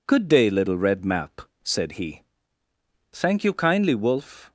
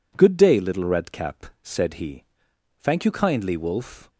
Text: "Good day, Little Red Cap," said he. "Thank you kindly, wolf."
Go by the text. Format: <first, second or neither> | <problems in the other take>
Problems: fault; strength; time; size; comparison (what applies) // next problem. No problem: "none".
second | says "Map" for "Cap"; at 1.0 s